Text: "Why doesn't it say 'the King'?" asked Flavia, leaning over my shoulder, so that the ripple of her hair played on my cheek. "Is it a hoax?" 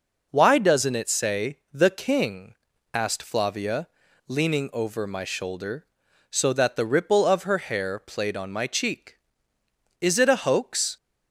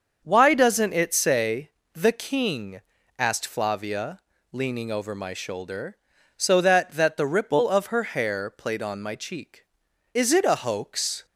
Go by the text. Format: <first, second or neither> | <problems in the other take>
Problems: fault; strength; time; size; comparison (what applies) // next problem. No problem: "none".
first | starts louder than the rest; until 1.2 s; 6.5 dB // pauses between "say" and "the"; slight; at 1.7 s; 0.20 s long // says "that" twice; at 6.9 s